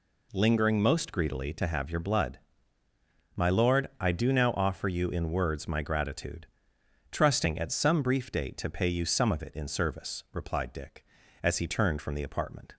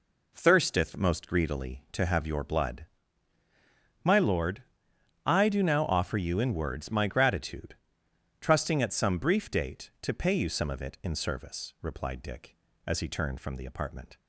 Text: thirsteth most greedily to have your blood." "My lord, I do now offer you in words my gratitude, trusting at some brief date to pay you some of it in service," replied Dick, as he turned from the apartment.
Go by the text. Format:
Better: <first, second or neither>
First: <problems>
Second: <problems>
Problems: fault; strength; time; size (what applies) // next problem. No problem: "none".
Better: second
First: says "lingering" for "thirsteth"; at 0.3 s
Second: none